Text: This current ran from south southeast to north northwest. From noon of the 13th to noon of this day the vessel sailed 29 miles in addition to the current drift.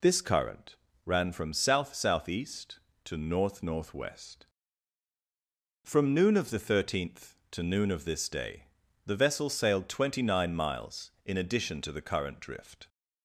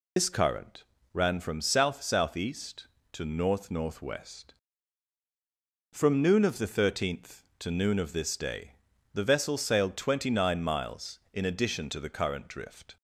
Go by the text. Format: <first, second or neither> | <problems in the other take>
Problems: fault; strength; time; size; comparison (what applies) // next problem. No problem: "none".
first | loses the start of "This"; at 0.1 s; 60 ms // pauses between "current" and "ran"; slight; at 0.8 s; 0.30 s long; slight in the first // pauses between "day" and "the"; at 8.7 s; 0.42 s long; also in the first